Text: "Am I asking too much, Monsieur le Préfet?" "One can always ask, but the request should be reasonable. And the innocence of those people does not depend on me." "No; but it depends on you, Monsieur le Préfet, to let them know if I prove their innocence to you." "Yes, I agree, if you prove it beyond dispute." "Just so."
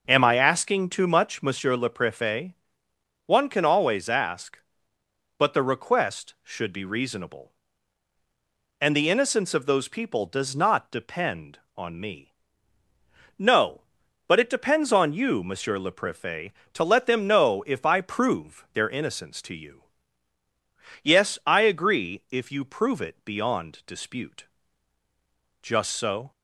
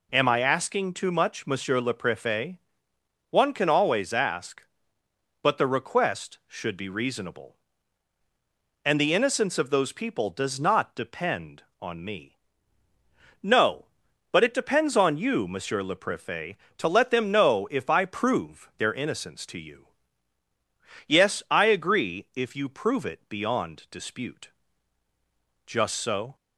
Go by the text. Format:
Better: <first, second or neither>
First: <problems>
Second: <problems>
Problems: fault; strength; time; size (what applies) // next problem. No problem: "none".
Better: second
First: starts louder than the rest; noticeable; until 1.6 s; 5.5 dB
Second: none